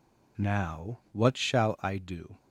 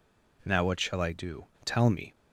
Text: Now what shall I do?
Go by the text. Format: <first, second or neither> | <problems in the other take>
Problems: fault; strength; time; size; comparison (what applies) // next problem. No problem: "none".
first | goes on to say "Tell me"; slight; from 1.6 s on; 0.48 s long